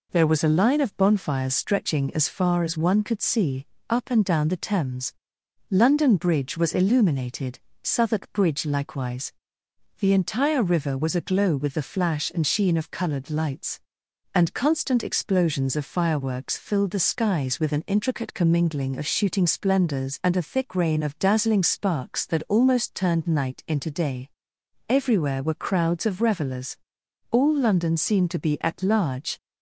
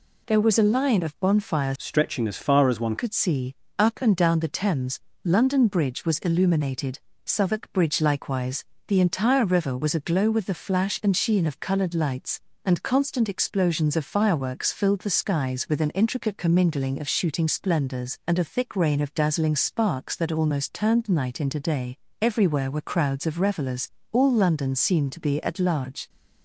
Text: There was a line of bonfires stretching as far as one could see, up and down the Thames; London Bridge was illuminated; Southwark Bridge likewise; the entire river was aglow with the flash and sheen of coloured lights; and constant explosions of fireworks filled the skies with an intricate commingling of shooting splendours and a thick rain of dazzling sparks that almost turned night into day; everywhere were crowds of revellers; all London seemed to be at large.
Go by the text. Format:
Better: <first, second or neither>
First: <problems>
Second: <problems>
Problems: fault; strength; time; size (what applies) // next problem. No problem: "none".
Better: first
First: none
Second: changes voice from "stretching" to "one"; from 1.7 to 2.9 s; 1.2 s long